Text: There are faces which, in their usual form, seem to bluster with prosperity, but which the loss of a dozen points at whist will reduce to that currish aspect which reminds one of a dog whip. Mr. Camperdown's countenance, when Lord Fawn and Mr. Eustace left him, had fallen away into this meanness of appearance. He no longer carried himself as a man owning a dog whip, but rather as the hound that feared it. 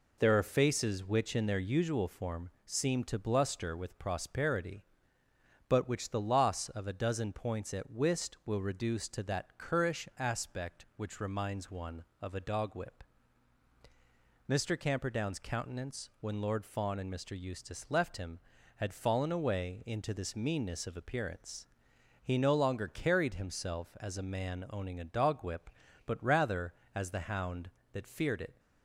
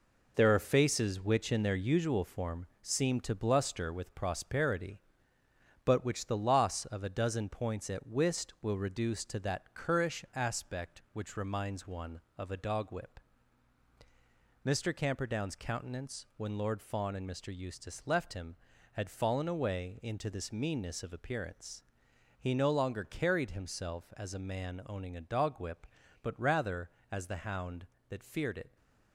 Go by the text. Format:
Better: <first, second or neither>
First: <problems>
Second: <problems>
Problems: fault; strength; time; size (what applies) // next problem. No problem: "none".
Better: first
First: none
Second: gets quieter; throughout; 6.5 dB